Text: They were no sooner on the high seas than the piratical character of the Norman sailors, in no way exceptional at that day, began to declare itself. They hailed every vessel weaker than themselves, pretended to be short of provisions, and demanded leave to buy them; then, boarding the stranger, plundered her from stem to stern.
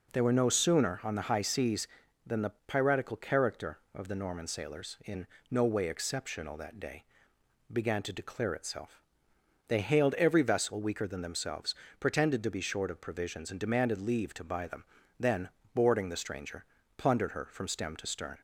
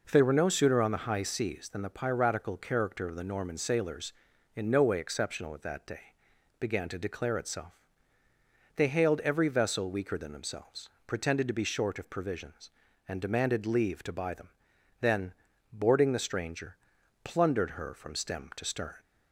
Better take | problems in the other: second | pauses between "the" and "piratical"; slight; at 2.5 s; 0.16 s long // pauses between "in" and "no"; slight; at 5.2 s; 0.24 s long // skips "at"; at 6.5 s

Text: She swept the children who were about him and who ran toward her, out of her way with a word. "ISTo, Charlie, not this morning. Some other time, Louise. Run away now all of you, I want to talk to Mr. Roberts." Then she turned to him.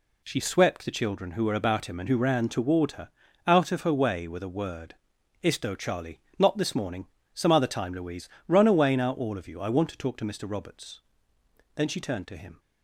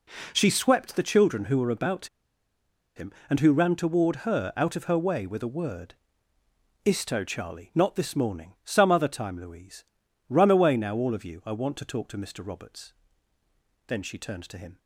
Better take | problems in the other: first | pauses between "about" and "him"; noticeable; at 2.0 s; 0.89 s long

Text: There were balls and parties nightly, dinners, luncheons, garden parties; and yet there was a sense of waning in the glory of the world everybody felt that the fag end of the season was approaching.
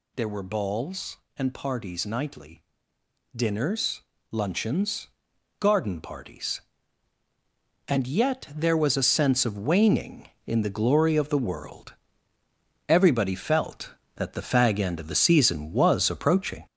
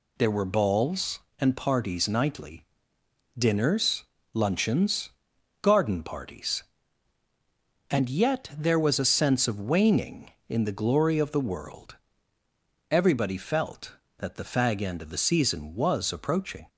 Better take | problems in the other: second | gets louder; noticeable; throughout; 4.5 dB // pauses between "world" and "everybody"; noticeable; at 11.9 s; 0.92 s long; noticeable in the second

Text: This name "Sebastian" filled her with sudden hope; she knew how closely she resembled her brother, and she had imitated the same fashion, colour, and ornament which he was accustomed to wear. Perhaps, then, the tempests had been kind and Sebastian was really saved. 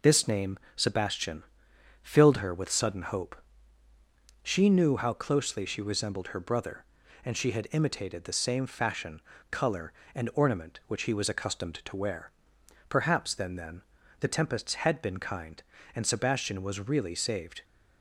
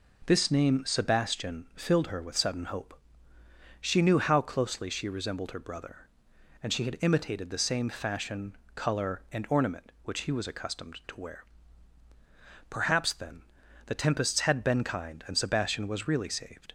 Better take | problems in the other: second | pauses between "name" and "Sebastian"; slight; at 0.5 s; 0.18 s long // pauses between "Sebastian" and "filled"; noticeable; at 1.4 s; 0.62 s long // says "then" twice; at 13.5 s

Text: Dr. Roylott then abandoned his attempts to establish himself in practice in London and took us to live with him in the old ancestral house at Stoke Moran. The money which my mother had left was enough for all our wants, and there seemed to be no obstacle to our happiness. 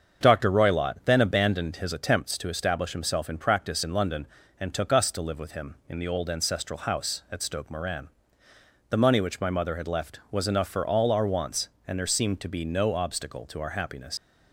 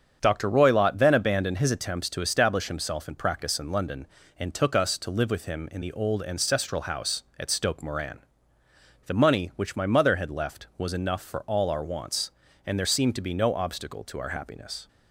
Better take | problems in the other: second | starts louder than the rest; strong; until 1.2 s; 7 dB; strong in the second // leaves "happiness" unfinished; at 14.1 s; 70 ms

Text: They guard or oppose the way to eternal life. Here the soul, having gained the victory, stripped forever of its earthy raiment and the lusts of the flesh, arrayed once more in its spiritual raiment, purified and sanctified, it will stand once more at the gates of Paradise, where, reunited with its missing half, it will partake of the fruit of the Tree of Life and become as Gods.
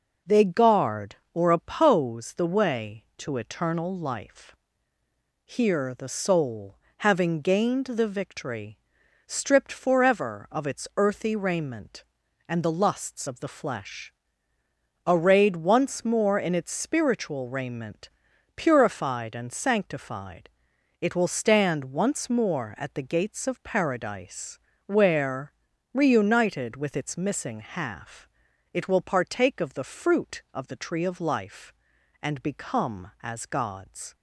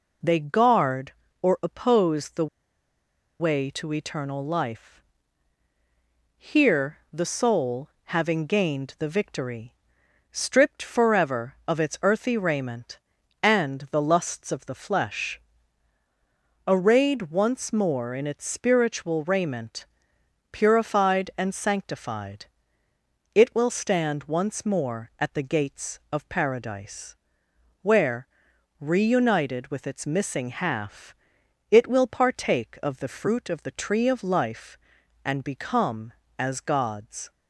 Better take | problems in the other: first | pauses between "the" and "way"; noticeable; at 2.4 s; 0.94 s long // pauses between "Here" and "the"; slight; at 6.9 s; 0.16 s long

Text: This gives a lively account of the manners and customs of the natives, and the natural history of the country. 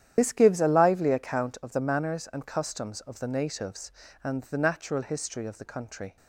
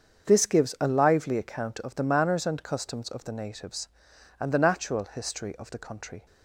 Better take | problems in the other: second | loses the start of "This"; at 0.1 s; 60 ms // starts louder than the rest; strong; until 1.1 s; 10.5 dB; also in the second

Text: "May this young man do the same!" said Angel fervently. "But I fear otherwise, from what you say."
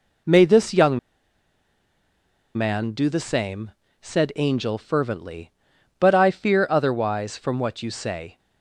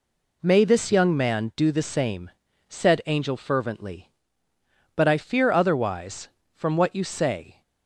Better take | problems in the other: second | pauses between "young" and "man"; strong; at 0.9 s; 1.5 s long

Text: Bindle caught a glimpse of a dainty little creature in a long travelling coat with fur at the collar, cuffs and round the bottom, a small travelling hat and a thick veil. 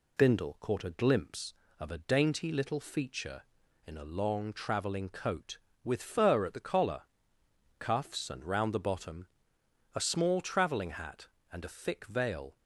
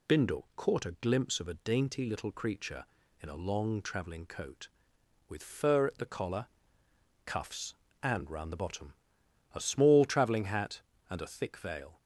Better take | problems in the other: second | says "feature" for "creature"; at 2.7 s

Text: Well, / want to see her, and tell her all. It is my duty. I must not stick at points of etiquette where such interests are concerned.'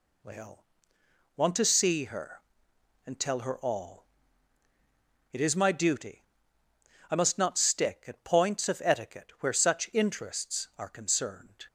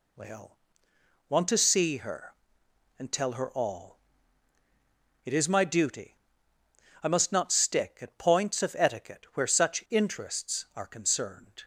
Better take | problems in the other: neither | none

